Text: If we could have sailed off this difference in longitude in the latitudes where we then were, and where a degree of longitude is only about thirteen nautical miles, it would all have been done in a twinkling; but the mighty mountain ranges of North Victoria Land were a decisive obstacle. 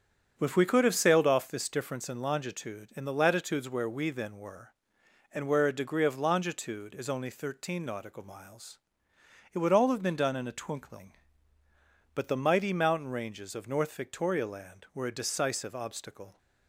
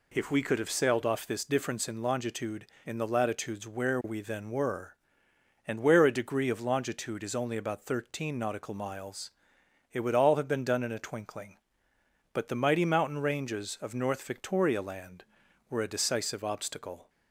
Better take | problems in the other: second | starts louder than the rest; strong; until 1.3 s; 7.5 dB // skips "about"; at 7.3 s

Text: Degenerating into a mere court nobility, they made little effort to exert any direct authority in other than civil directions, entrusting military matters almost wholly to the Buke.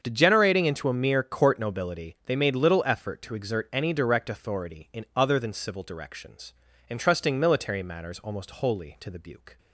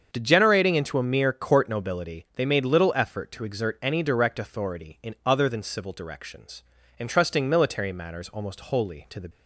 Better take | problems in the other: first | starts louder than the rest; until 1.1 s; 7 dB; also in the first // stops before "Buke"; at 9.3 s

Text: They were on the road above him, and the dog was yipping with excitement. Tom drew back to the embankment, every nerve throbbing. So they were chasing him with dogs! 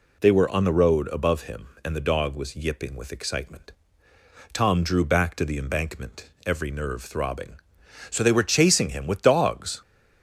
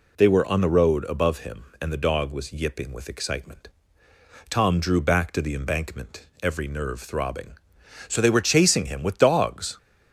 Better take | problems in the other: neither | none

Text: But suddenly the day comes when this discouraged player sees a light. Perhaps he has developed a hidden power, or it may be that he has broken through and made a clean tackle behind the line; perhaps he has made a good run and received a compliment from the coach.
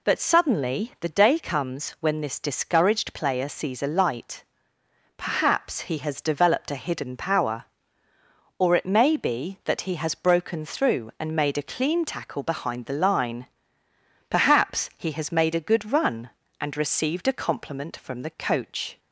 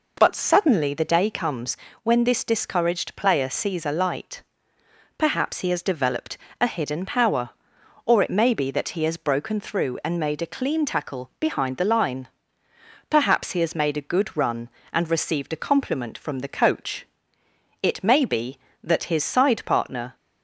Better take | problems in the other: first | pauses between "comes" and "when"; slight; at 1.7 s; 0.26 s long // pauses between "developed" and "a"; slight; at 6.3 s; 0.22 s long // goes on to say "It may be that his side partner"; strong; from 17.8 s on; 2.3 s long

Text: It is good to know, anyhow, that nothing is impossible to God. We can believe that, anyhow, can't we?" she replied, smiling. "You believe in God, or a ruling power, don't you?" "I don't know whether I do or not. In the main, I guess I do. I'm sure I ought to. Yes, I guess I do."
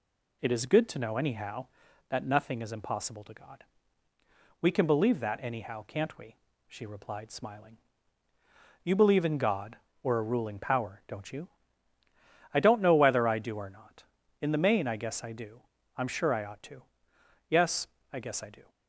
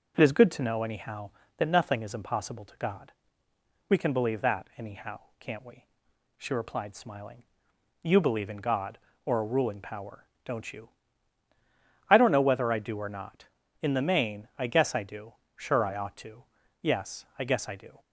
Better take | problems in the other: first | skips "I'm"; at 15.4 s

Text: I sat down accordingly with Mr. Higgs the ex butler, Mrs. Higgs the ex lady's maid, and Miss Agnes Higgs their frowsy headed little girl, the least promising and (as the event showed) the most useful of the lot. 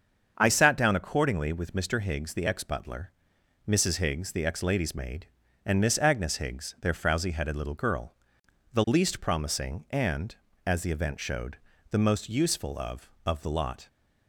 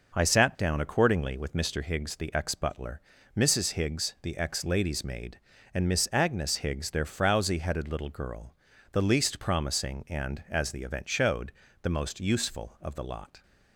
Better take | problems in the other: second | starts louder than the rest; until 1.3 s; 7 dB // says "of" twice; at 13.2 s

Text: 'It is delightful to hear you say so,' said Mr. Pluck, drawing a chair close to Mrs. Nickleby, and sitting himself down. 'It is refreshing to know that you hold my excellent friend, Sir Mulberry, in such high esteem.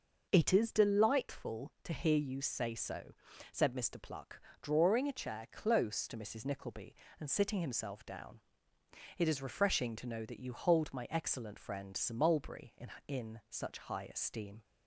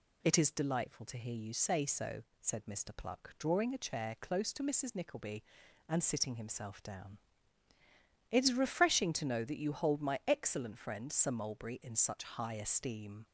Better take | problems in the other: second | says "in" twice; at 13.0 s

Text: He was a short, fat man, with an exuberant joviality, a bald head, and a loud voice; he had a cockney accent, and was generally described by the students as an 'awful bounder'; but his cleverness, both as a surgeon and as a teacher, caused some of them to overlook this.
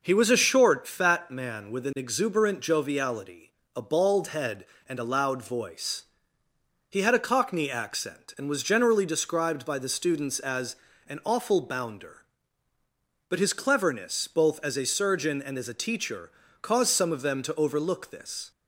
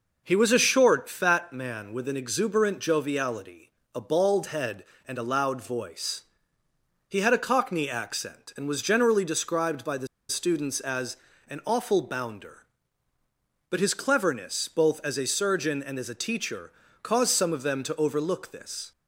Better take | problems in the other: first | pauses between "the" and "students"; slight; at 10.0 s; 0.22 s long // pauses between "as" and "an"; slight; at 11.1 s; 0.32 s long; slight in the first

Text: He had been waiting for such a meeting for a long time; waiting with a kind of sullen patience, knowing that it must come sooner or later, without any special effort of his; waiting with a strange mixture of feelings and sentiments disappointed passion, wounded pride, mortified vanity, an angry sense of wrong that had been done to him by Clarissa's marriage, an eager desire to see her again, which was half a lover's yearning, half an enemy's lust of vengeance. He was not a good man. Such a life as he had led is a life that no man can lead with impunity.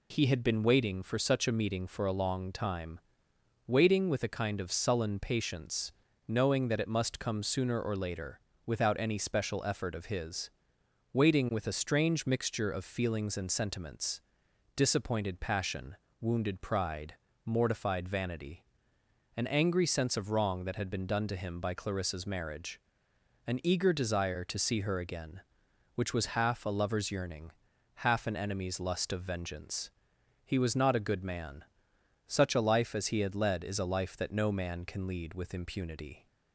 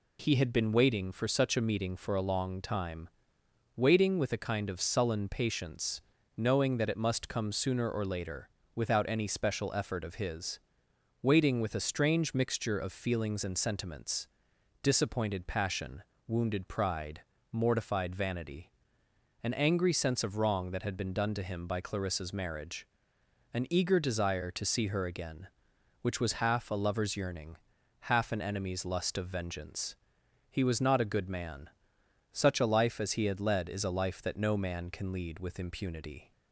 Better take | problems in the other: neither | pauses between "sentiments" and "disappointed"; noticeable; the same in both

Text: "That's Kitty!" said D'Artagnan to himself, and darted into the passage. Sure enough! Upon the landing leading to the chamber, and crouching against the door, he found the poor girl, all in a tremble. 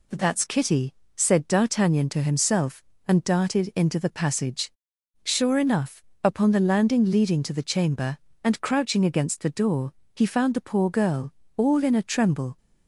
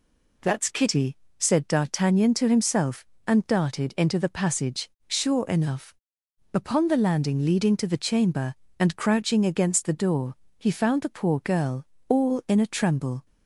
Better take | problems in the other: neither | none

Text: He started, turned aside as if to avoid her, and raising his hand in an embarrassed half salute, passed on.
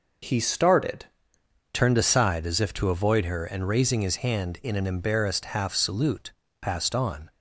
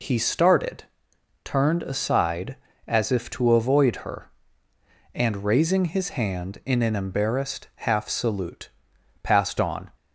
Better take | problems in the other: second | changes voice at "turned"; from 1.7 s on; 5.5 s long

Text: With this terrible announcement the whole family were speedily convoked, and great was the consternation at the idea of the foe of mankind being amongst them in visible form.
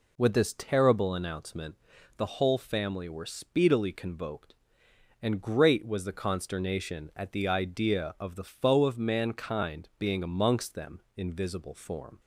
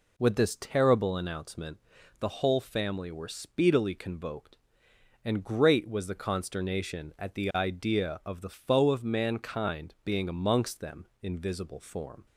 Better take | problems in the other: neither | pauses between "announcement" and "the"; the same in both

